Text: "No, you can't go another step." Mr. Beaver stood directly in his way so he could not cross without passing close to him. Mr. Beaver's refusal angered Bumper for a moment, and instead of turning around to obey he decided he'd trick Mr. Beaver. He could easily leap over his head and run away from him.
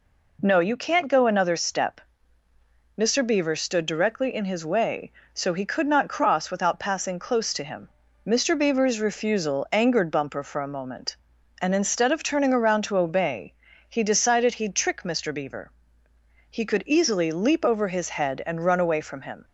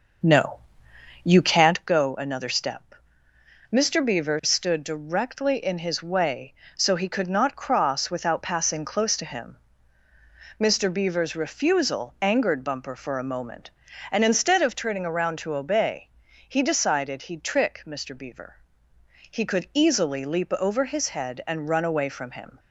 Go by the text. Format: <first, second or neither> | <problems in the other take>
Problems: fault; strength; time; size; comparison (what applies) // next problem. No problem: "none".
first | starts louder than the rest; noticeable; until 1.9 s; 6 dB // pauses between "obey" and "he"; at 16.0 s; 0.40 s long; slight in the first